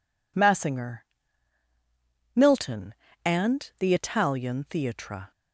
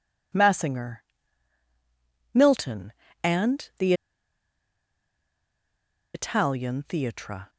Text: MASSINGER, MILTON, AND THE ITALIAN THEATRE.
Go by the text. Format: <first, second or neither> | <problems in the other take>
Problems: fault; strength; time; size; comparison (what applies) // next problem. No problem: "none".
first | pauses between "THE" and "ITALIAN"; strong; at 3.9 s; 2.2 s long